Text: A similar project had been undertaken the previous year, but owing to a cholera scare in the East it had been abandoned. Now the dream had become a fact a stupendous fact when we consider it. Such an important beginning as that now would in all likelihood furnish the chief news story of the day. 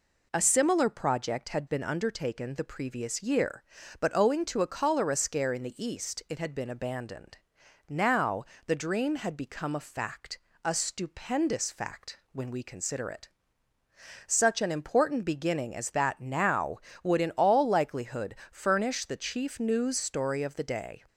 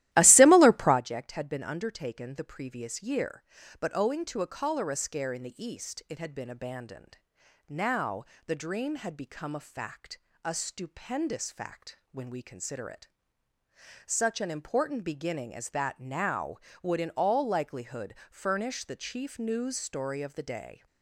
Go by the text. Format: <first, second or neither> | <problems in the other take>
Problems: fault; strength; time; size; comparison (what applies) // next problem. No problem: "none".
first | starts louder than the rest; strong; until 1.0 s; 15 dB // pauses between "Now" and "the"; slight; at 8.2 s; 0.22 s long; slight in the first // pauses between "fact" and "a"; slight; at 10.1 s; 0.26 s long; slight in the first // pauses between "likelihood" and "furnish"; slight; at 18.1 s; 0.16 s long; slight in the first